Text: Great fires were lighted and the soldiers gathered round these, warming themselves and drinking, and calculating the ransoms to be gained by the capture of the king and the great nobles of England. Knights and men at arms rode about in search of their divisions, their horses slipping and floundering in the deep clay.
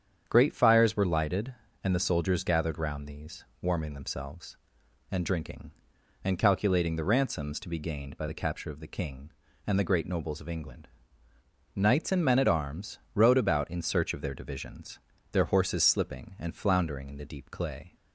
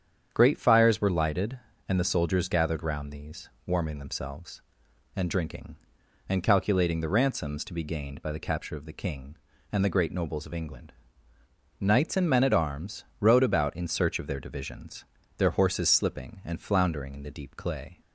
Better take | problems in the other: neither | starts louder than the rest; strong; the same in both // pauses between "arms" and "rode"; slight; the same in both

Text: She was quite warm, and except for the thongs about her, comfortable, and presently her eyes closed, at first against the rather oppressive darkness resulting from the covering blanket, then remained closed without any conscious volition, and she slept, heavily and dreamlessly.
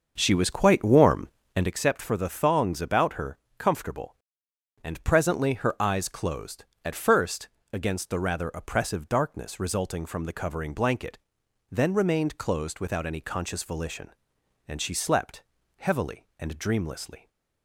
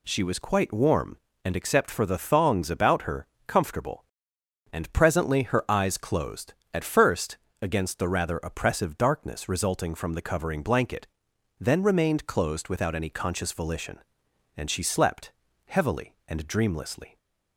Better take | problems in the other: second | starts louder than the rest; until 1.8 s; 6.5 dB // pauses between "first" and "against"; slight; at 7.4 s; 0.24 s long; slight in the second

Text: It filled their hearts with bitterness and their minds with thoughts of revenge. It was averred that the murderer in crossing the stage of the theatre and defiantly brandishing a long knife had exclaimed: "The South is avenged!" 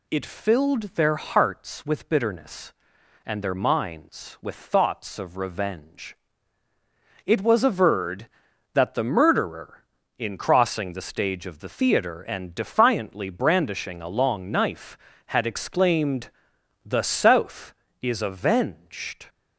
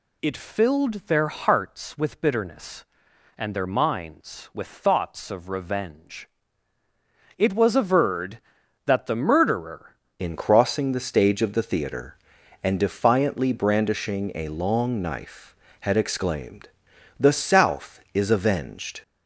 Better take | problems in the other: first | changes voice at "in"; from 10.1 s on; 8.9 s long

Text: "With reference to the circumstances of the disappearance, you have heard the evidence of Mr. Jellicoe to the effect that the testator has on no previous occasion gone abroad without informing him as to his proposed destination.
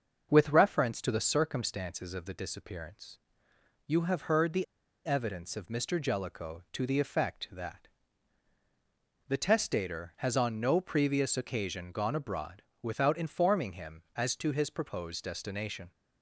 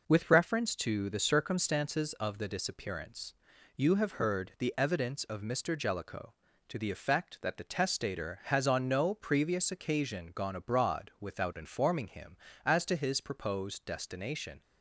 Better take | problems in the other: second | starts louder than the rest; until 1.3 s; 6.5 dB // pauses between "the" and "evidence"; at 4.6 s; 0.41 s long // pauses between "that" and "the"; strong; at 7.8 s; 1.3 s long // pauses between "abroad" and "without"; slight; at 12.6 s; 0.20 s long

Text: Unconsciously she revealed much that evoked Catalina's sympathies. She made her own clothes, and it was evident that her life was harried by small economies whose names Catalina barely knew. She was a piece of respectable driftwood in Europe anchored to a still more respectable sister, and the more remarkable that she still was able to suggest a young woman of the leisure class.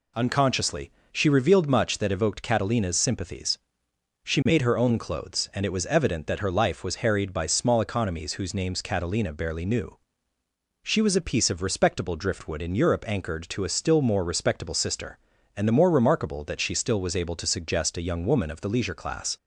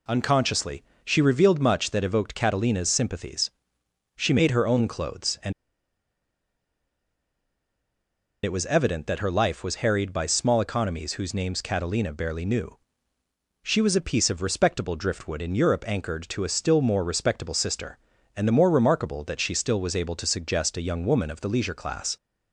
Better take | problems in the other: first | pauses between "Unconsciously" and "she"; slight; at 0.8 s; 0.20 s long; slight in the first // pauses between "and" and "it"; strong; at 5.5 s; 2.9 s long

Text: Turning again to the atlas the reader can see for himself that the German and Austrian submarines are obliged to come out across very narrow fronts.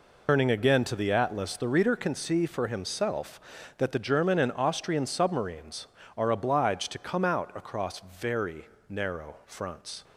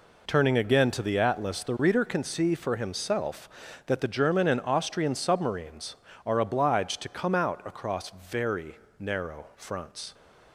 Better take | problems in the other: second | loses the start of "Turning"; at 0.2 s; 80 ms // pauses between "very" and "narrow"; slight; at 8.6 s; 0.22 s long; slight in the second

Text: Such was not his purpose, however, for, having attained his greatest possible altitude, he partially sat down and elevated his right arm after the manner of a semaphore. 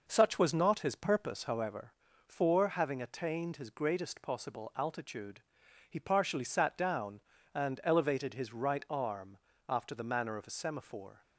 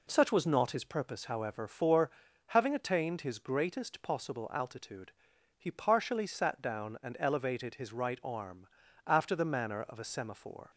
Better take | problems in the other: second | starts louder than the rest; noticeable; until 1.7 s; 5.5 dB // pauses between "arm" and "after"; slight; at 9.3 s; 0.30 s long; also in the second

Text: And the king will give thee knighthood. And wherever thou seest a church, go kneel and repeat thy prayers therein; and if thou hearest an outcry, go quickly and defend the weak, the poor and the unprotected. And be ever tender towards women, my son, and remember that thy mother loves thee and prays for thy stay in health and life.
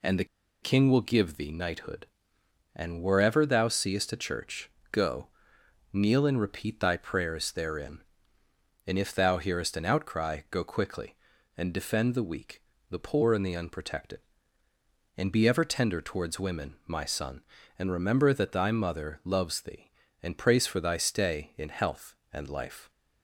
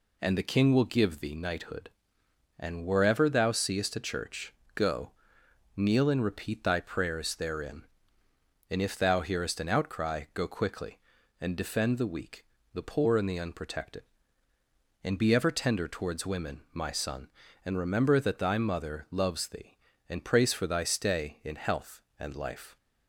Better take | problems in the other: second | pauses between "the" and "king"; at 0.2 s; 0.37 s long // pauses between "go" and "kneel"; noticeable; at 5.2 s; 0.68 s long; noticeable in the second

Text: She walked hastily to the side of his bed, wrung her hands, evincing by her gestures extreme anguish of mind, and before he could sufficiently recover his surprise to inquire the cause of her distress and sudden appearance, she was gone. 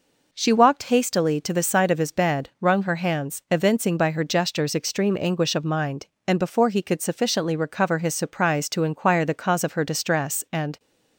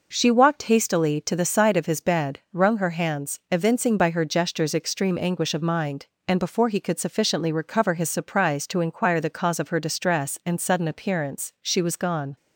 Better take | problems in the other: second | stops before "sudden appearance she was gone"; at 10.7 s

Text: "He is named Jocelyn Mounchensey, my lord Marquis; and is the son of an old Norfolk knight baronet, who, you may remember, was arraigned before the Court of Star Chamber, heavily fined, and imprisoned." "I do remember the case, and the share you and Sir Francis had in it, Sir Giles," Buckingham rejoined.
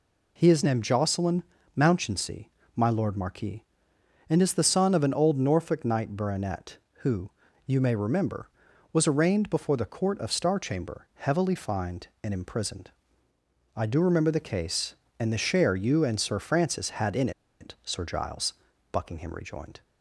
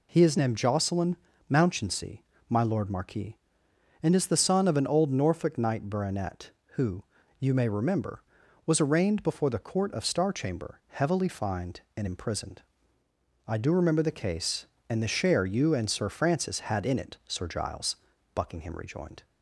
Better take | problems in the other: second | pauses between "Jocelyn" and "Mounchensey"; slight; at 1.4 s; 0.32 s long; slight in the second // pauses between "in" and "it"; slight; at 17.3 s; 0.29 s long

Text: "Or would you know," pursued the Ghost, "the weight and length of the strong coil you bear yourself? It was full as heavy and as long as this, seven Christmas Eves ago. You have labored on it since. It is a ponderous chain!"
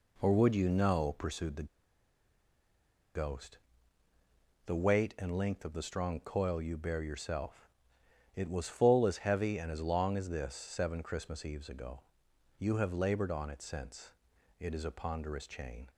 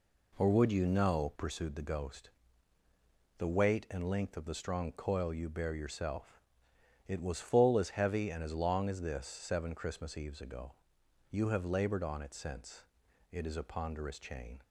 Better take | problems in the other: second | pauses between "the" and "Ghost"; strong; at 1.6 s; 1.4 s long

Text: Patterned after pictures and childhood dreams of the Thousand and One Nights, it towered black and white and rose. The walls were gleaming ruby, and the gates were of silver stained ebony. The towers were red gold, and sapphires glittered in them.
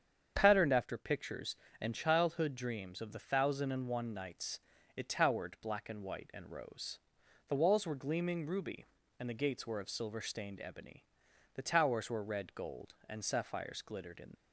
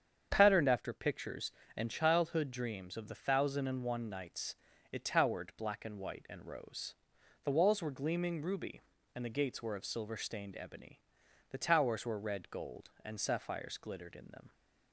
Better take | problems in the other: second | starts louder than the rest; strong; until 1.3 s; 8 dB; strong in the second // stops before "them"; at 14.3 s

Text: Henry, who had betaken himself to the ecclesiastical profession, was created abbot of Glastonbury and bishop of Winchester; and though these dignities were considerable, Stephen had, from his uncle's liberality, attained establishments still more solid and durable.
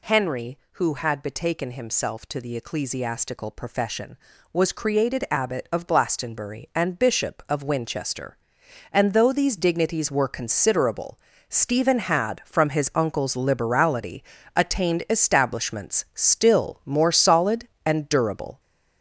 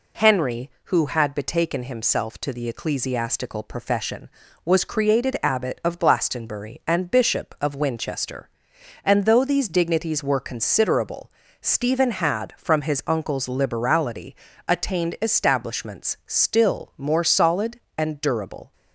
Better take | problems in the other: second | gets louder; noticeable; throughout; 5.5 dB

